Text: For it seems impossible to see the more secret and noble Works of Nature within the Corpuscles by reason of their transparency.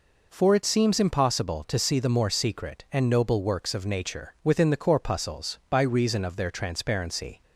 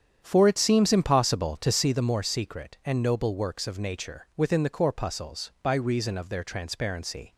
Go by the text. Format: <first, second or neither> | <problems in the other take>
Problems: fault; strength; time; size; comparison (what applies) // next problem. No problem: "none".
first | starts louder than the rest; strong; until 2.1 s; 8.5 dB